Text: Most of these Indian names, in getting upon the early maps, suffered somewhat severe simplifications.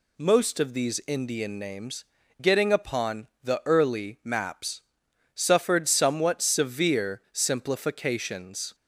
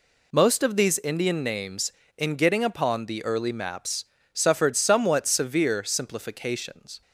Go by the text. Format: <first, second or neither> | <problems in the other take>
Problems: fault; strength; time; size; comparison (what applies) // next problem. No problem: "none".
second | skips "in"; at 2.2 s